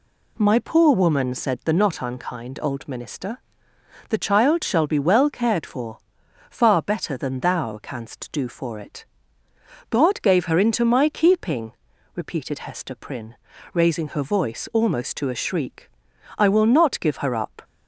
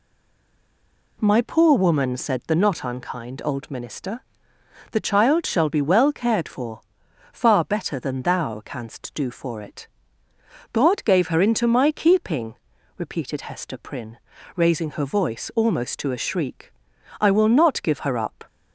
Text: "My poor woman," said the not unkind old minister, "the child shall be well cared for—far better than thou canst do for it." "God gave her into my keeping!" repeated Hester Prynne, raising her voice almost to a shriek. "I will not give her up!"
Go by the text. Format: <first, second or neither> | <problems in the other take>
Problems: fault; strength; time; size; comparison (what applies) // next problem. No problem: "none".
first | stays silent before the first word; noticeable; until 1.1 s; 1.1 s long